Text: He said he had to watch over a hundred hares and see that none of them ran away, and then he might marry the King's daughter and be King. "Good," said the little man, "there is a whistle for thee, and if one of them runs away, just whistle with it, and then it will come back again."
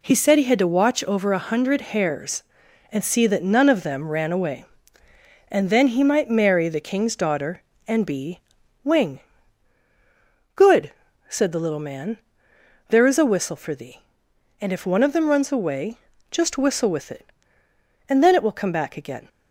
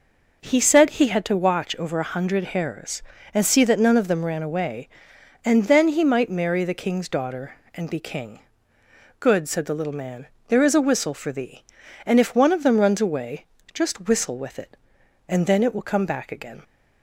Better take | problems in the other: second | says "Wing" for "King"; at 8.8 s

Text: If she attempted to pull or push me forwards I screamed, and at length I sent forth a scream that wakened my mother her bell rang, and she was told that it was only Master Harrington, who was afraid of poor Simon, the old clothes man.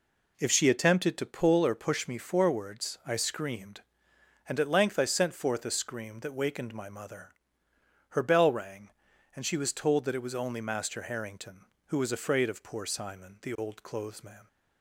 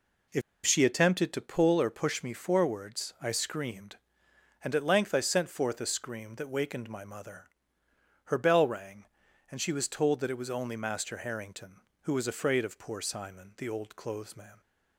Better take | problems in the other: first | pauses between "If" and "she"; slight; at 0.4 s; 0.24 s long // pauses between "mother" and "her"; noticeable; at 7.4 s; 0.78 s long; noticeable in the first

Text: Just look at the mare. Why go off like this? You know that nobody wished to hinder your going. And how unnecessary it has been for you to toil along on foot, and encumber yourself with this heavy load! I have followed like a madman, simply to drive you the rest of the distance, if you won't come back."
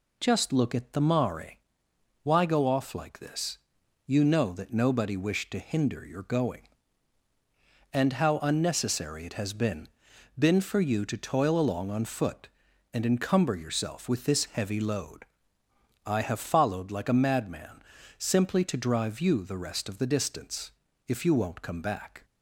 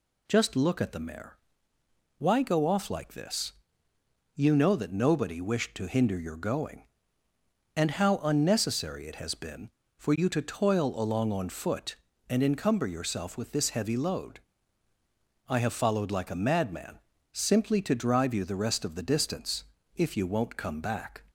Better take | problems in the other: second | says "been" twice; at 10.3 s

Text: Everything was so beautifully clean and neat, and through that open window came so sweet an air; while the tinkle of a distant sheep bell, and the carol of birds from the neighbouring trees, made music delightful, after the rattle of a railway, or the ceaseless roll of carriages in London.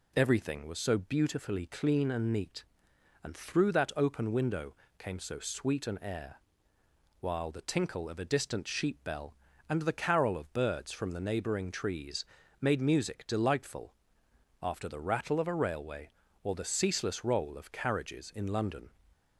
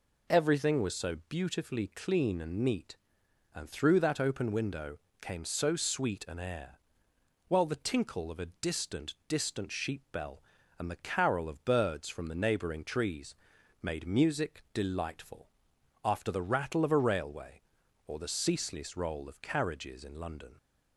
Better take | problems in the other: first | pauses between "window" and "came"; slight; at 4.9 s; 0.24 s long; slight in the first // says "distant" twice; at 9.2 s

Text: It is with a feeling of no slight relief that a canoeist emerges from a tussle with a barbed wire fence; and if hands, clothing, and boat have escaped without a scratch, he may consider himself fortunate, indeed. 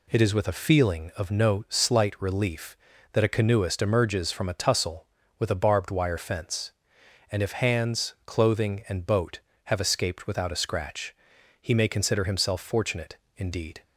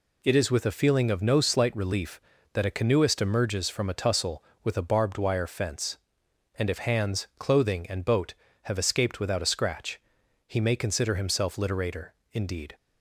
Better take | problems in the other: first | says "literator" for "fortunate"; at 11.5 s

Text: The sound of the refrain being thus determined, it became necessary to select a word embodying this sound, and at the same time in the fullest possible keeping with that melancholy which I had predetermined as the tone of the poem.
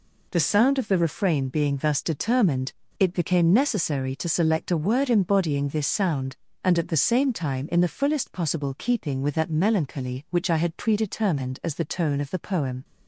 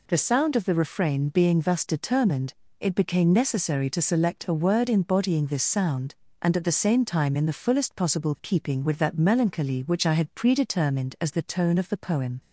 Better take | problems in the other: neither | none

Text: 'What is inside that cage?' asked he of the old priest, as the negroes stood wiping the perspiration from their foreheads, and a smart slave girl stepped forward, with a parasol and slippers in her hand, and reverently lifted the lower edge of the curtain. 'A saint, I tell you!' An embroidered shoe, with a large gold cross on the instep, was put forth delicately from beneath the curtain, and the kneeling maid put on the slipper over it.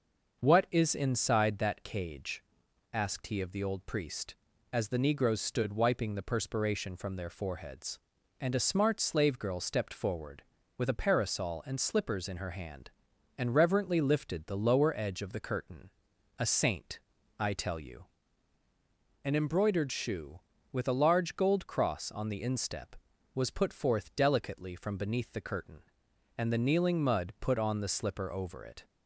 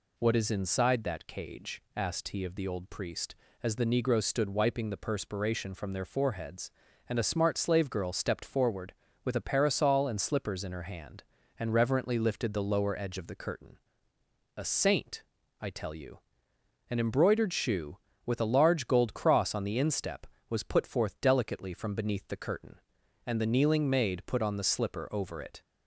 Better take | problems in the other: second | starts louder than the rest; until 1.4 s; 6.5 dB // says "mud" for "maid"; at 27.0 s

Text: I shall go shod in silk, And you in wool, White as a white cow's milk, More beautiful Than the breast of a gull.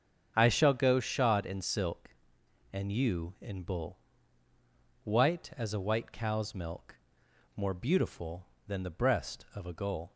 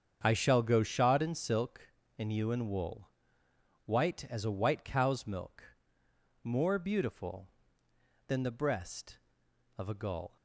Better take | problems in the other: second | starts louder than the rest; until 1.3 s; 7 dB; strong in the second // says "bull" for "wool"; at 3.6 s

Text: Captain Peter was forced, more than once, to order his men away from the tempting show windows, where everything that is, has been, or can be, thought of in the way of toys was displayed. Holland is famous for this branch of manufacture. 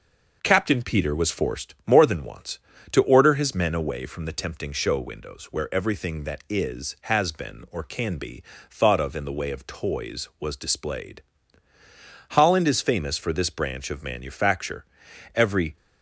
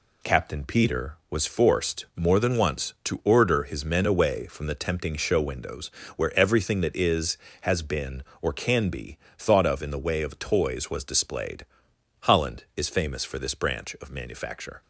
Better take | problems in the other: second | goes on to say "Every"; slight; from 15.3 s on; 0.42 s long

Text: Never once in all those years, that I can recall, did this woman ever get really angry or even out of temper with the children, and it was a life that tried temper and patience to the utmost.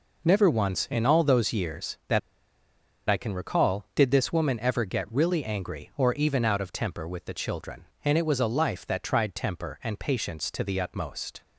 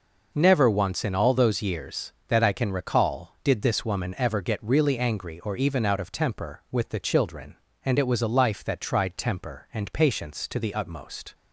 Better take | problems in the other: second | pauses between "that" and "I"; noticeable; at 2.1 s; 0.87 s long

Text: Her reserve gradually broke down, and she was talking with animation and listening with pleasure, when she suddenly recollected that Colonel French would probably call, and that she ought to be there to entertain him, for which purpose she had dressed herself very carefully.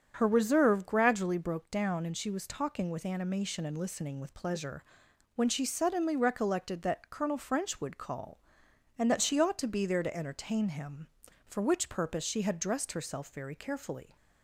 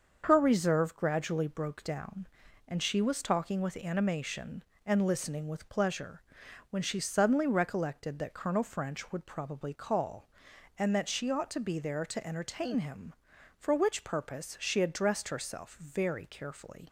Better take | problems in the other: second | starts louder than the rest; strong; until 1.1 s; 7 dB; also in the second // skips "probably"; at 7.9 s

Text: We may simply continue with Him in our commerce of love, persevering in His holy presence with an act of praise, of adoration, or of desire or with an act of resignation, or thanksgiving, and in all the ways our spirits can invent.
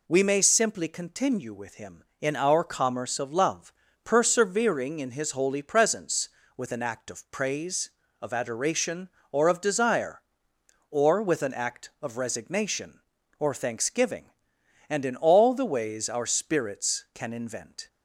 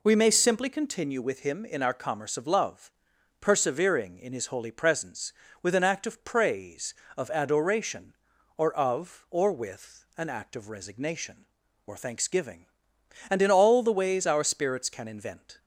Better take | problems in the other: first | skips "desire"; at 9.2 s

